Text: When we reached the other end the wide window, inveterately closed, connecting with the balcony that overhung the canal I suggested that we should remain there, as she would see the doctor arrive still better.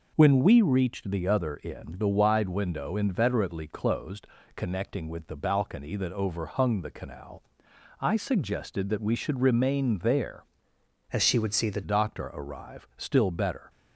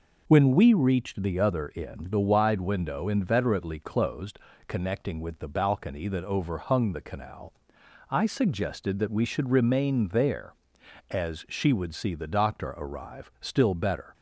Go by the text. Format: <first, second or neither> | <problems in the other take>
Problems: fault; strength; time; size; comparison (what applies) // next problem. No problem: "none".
second | pauses between "canal" and "I"; noticeable; at 7.4 s; 0.60 s long; noticeable in the second // changes voice from "as" to "the"; from 11.1 to 11.8 s; 0.7 s long